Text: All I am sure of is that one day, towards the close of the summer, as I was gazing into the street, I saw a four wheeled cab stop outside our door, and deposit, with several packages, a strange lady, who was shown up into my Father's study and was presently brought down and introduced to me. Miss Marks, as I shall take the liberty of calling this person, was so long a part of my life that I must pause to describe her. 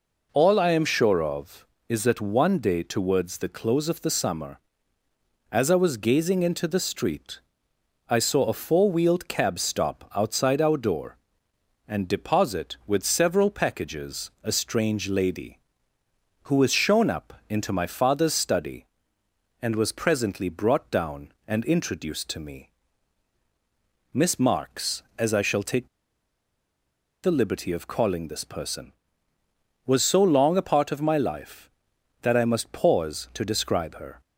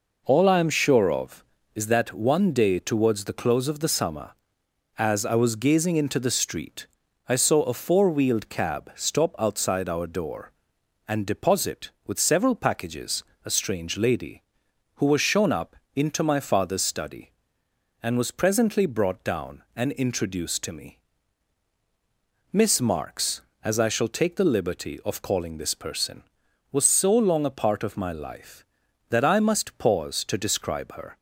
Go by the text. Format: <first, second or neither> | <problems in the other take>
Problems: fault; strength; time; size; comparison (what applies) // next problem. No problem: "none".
second | pauses between "up" and "into"; slight; at 17.3 s; 0.16 s long; slight in the second // pauses between "take" and "the"; strong; at 25.8 s; 1.3 s long